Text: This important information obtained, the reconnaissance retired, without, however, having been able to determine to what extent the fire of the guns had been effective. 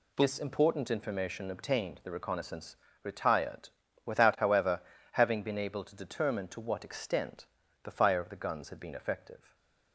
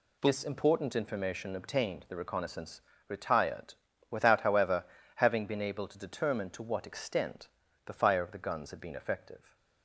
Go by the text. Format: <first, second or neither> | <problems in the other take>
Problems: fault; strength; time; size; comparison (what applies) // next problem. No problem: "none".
neither | pauses between "reconnaissance" and "retired"; slight; the same in both // pauses between "extent" and "the"; slight; the same in both